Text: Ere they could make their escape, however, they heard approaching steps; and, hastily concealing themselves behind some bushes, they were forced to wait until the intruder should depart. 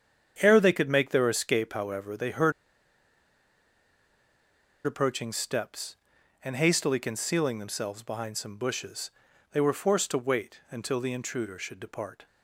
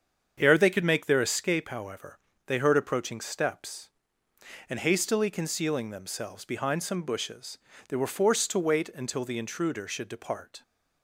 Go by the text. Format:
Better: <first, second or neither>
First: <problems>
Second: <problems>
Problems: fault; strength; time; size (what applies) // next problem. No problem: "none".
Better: second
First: starts louder than the rest; strong; until 1.4 s; 8 dB // pauses between "heard" and "approaching"; strong; at 2.5 s; 2.3 s long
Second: starts louder than the rest; strong; until 1.4 s; 7.5 dB